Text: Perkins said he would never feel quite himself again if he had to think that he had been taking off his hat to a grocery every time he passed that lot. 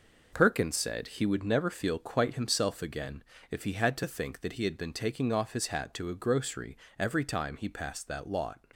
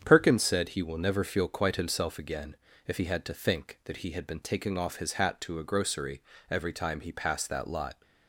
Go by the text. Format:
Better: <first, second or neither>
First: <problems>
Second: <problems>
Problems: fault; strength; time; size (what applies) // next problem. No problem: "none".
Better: first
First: pauses between "again" and "if"; slight; at 3.2 s; 0.30 s long // pauses between "grocery" and "every"; slight; at 6.7 s; 0.22 s long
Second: starts louder than the rest; strong; until 1.0 s; 8 dB // says "will" for "would"; at 0.8 s // pauses between "again" and "if"; slight; at 2.5 s; 0.32 s long // pauses between "grocery" and "every"; slight; at 6.2 s; 0.28 s long